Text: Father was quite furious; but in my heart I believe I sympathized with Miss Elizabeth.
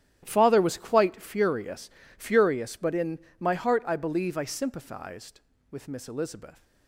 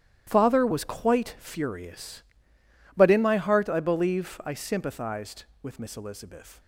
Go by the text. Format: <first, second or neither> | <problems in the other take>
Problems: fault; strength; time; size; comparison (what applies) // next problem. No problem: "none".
second | starts louder than the rest; strong; until 1.2 s; 12 dB; strong in the second // says "furious" twice; at 2.1 s // pauses between "in" and "my"; slight; at 3.1 s; 0.20 s long